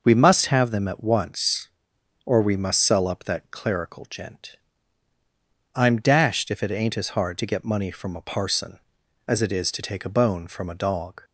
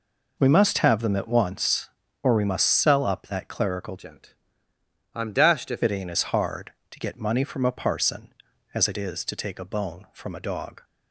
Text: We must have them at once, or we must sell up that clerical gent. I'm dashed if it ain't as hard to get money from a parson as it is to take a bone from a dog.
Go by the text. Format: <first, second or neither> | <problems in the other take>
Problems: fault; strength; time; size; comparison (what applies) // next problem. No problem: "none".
first | changes voice from "gent" to "if"; from 3.9 to 5.8 s; 1.9 s long